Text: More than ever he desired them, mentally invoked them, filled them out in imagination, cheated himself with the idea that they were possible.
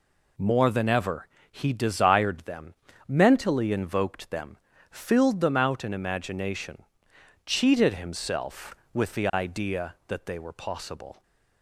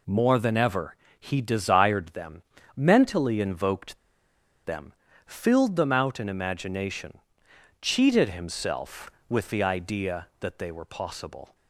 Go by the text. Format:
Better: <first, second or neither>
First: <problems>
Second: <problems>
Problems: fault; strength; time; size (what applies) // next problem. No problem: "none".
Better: first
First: pauses between "ever" and "he"; slight; at 1.2 s; 0.24 s long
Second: pauses between "ever" and "he"; slight; at 0.9 s; 0.24 s long // pauses between "invoked" and "them"; noticeable; at 3.9 s; 0.67 s long